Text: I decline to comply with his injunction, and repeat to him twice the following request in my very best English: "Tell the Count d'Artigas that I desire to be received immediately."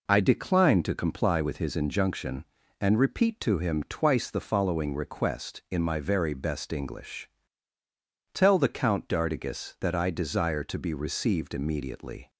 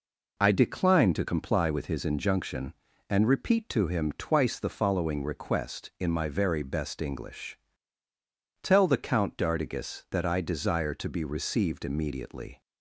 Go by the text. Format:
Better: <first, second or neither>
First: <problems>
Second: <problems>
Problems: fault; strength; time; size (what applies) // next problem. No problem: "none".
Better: neither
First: none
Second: none